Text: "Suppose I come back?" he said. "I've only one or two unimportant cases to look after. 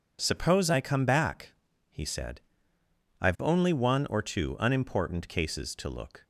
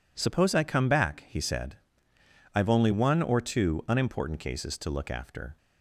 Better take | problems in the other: second | stops before "after"; at 6.2 s

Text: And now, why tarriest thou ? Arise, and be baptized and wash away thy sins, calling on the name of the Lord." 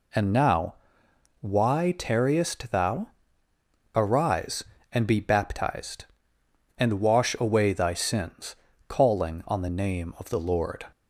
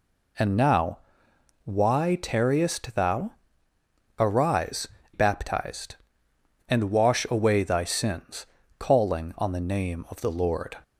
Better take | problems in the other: first | skips "and be"; at 5.0 s

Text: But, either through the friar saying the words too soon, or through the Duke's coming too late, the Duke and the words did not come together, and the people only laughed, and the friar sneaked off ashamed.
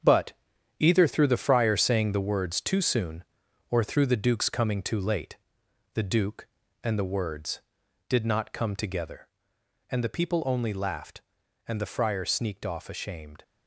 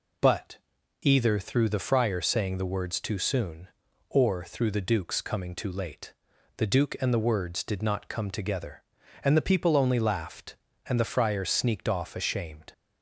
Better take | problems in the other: second | gets quieter; strong; throughout; 8.5 dB

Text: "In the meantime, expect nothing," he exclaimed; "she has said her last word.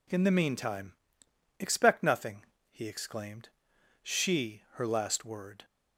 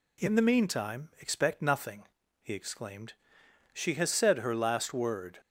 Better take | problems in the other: second | skips "has said"; at 4.6 s

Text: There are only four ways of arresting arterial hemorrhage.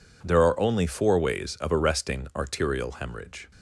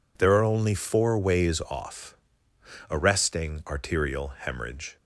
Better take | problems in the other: first | says "off" for "of"; at 1.6 s

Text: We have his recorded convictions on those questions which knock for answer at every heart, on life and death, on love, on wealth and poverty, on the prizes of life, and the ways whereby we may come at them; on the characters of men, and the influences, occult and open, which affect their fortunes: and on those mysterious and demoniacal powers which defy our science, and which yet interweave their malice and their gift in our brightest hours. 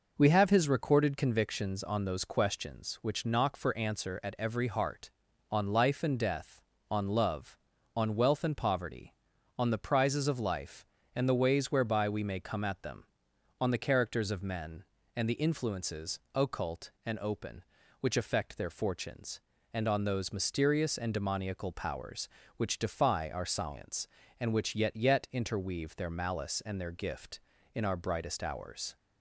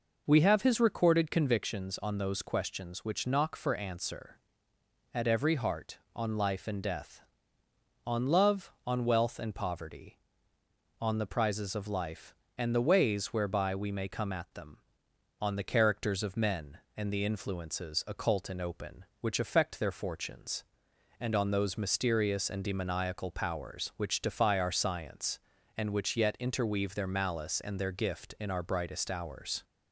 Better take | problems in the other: second | says "yet" twice; at 24.9 s

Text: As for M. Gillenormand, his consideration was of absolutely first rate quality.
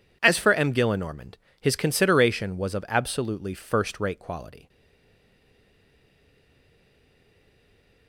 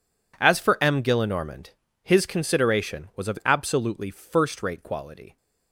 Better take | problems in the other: second | stays silent after the last word; strong; from 4.6 s on; 3.4 s long

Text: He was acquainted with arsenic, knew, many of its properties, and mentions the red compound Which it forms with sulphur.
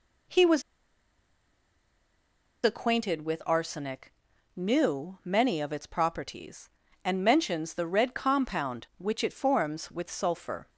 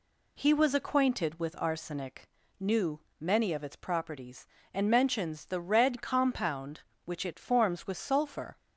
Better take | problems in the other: second | pauses between "was" and "acquainted"; strong; at 0.6 s; 2.0 s long

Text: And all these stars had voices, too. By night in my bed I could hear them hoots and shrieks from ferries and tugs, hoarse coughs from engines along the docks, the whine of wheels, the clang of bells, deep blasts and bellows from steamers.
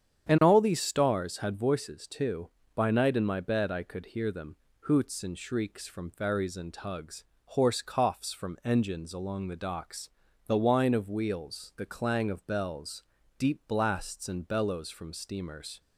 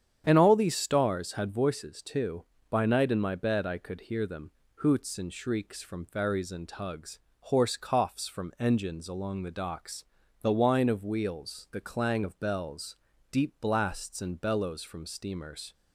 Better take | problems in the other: neither | starts louder than the rest; strong; the same in both // pauses between "them" and "hoots"; slight; the same in both

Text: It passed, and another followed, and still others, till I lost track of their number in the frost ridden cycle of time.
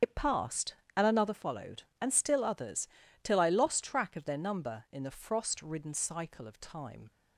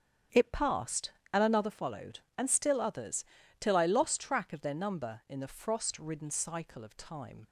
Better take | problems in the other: second | loses the start of "It"; at 0.0 s; 75 ms // starts louder than the rest; strong; until 1.2 s; 7.5 dB; strong in the second

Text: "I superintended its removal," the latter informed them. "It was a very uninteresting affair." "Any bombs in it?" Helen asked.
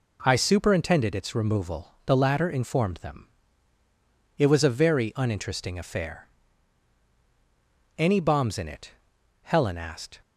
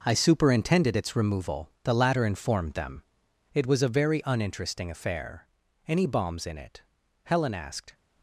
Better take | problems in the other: first | gets quieter; strong; throughout; 10.5 dB

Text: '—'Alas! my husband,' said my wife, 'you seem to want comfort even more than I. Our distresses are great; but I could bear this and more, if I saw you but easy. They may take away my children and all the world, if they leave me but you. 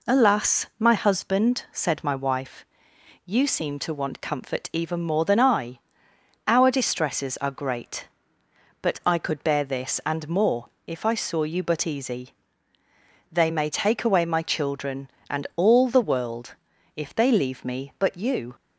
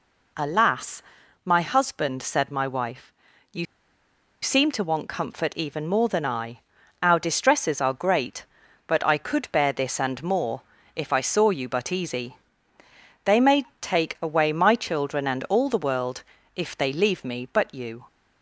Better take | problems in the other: first | pauses between "you" and "seem"; noticeable; at 3.6 s; 0.78 s long // pauses between "may" and "take"; slight; at 13.6 s; 0.16 s long

